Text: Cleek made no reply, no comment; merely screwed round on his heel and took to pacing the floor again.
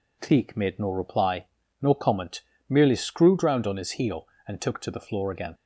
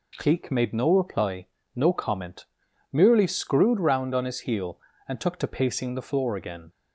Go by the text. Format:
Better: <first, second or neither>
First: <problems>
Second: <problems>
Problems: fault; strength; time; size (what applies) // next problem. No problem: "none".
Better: second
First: skips "pacing"; at 4.8 s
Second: none